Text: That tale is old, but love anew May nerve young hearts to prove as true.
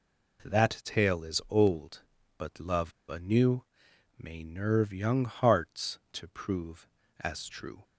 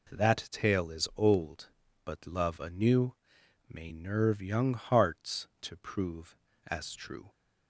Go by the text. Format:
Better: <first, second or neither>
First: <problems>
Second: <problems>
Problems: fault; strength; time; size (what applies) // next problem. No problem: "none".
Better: second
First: pauses between "love" and "anew"; slight; at 2.9 s; 0.19 s long // pauses between "anew" and "May"; noticeable; at 3.6 s; 0.54 s long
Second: pauses between "anew" and "May"; noticeable; at 3.1 s; 0.54 s long